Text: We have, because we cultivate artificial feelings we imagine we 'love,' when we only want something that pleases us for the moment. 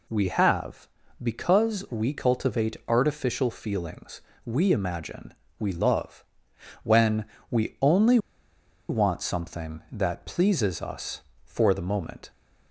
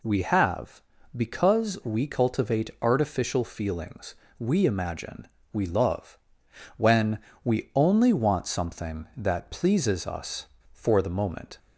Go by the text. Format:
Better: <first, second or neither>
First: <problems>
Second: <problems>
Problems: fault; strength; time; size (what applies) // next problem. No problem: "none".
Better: second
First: pauses between "feelings" and "we"; slight; at 4.2 s; 0.24 s long // pauses between "imagine" and "we"; slight; at 5.3 s; 0.26 s long // pauses between "when" and "we"; slight; at 7.2 s; 0.24 s long // pauses between "only" and "want"; noticeable; at 8.1 s; 0.71 s long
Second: pauses between "feelings" and "we"; slight; at 4.1 s; 0.24 s long // pauses between "imagine" and "we"; slight; at 5.2 s; 0.26 s long // pauses between "when" and "we"; slight; at 7.1 s; 0.24 s long